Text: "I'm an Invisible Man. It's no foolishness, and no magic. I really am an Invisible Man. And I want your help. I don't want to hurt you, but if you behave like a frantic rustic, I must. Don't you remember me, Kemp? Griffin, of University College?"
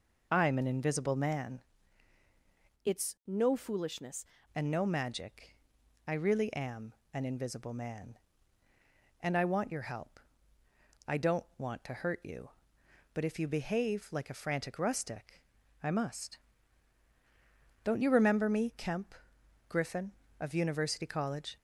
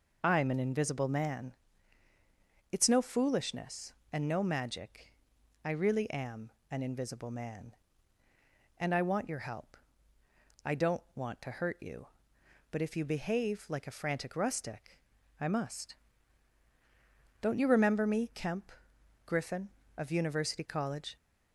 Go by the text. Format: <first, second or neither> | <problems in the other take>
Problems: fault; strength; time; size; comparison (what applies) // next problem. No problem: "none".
second | changes voice from "It's" to "foolishness"; from 2.8 to 4.2 s; 1.4 s long // pauses between "am" and "an"; slight; at 6.9 s; 0.20 s long; slight in the second